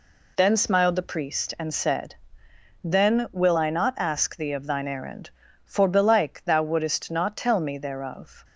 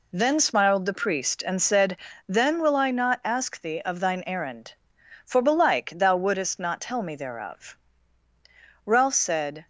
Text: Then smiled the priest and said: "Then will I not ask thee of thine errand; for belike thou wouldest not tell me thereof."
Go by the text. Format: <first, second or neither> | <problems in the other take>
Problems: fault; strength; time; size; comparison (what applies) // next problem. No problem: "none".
first | goes on to say "Ralph said"; noticeable; from 8.8 s on; 0.82 s long